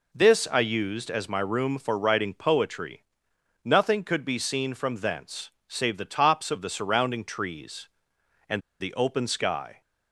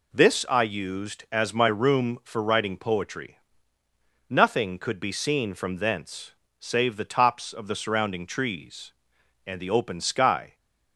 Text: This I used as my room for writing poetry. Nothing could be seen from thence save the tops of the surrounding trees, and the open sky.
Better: second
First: pauses between "thence" and "save"; slight; at 5.5 s; 0.18 s long // pauses between "and" and "the"; slight; at 8.6 s; 0.19 s long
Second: pauses between "thence" and "save"; slight; at 6.3 s; 0.28 s long

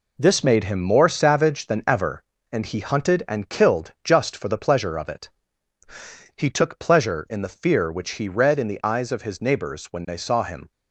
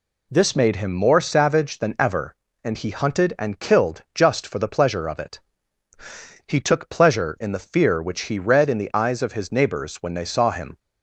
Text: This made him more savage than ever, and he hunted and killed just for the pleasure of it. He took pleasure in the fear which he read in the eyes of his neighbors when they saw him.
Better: second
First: gets quieter; throughout; 7 dB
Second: none

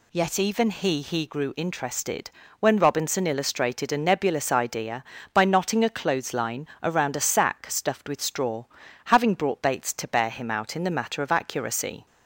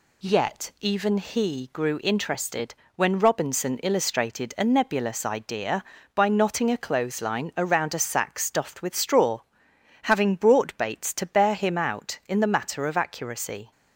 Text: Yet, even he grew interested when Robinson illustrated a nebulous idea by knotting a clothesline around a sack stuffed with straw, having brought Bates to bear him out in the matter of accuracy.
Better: second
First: says "he" twice; at 1.0 s // pauses between "interested" and "when"; slight; at 2.3 s; 0.28 s long // pauses between "clothesline" and "around"; slight; at 6.6 s; 0.16 s long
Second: pauses between "interested" and "when"; slight; at 2.7 s; 0.20 s long

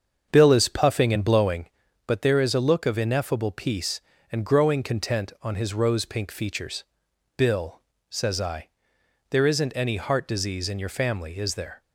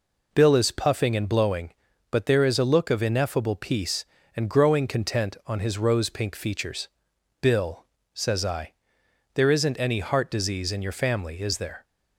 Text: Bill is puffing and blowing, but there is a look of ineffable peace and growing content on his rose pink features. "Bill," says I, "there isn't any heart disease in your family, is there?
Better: second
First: starts louder than the rest; until 1.8 s; 7 dB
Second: none

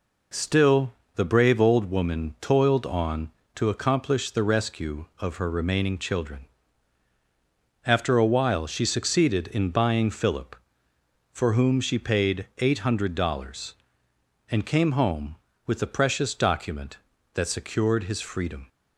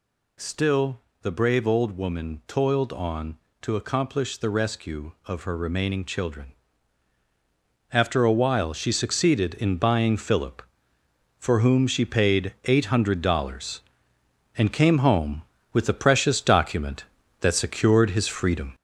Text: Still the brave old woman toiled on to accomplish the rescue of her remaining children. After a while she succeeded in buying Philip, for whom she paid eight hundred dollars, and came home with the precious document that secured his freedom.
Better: first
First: pauses between "Still" and "the"; slight; at 0.9 s; 0.22 s long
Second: gets louder; noticeable; throughout; 5.5 dB // pauses between "Still" and "the"; slight; at 1.0 s; 0.22 s long

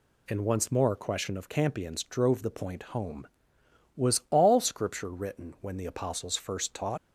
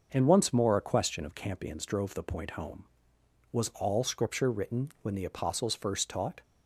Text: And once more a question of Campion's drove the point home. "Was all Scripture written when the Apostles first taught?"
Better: second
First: leaves "taught" unfinished; at 6.9 s; 95 ms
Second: none

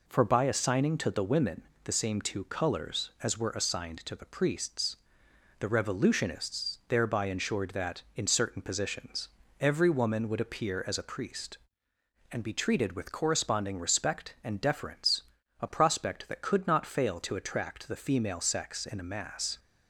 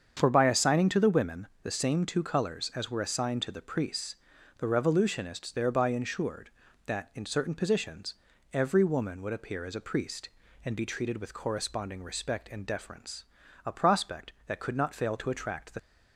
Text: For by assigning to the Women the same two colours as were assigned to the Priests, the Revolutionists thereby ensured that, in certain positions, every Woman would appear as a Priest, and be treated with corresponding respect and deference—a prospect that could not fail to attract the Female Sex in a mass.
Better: first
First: pauses between "Women" and "the"; slight; at 1.6 s; 0.22 s long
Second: starts louder than the rest; strong; until 1.1 s; 7.5 dB // pauses between "Women" and "the"; slight; at 1.4 s; 0.16 s long // stops before "Female Sex in a mass"; at 15.7 s

